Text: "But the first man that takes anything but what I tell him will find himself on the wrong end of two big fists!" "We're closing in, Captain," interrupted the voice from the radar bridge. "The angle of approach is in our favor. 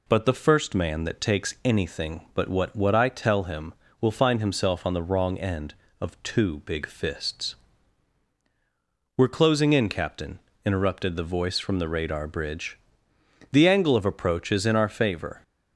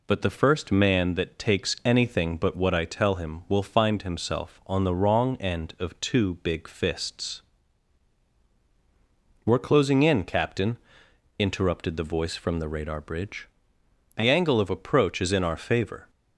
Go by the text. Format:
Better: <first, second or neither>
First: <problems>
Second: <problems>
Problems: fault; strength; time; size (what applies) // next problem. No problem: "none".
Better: second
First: says "what" twice; at 2.7 s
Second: none